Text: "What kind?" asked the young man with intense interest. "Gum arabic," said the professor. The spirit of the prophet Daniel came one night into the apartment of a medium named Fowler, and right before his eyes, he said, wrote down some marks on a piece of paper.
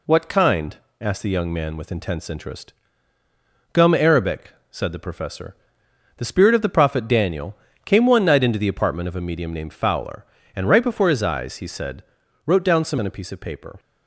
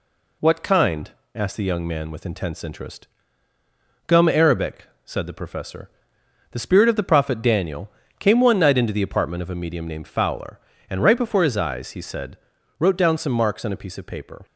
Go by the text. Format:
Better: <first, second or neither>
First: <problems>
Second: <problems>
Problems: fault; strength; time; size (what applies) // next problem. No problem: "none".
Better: second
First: pauses between "Daniel" and "came"; slight; at 7.5 s; 0.26 s long // skips "marks"; at 12.9 s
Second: pauses between "Daniel" and "came"; slight; at 7.9 s; 0.26 s long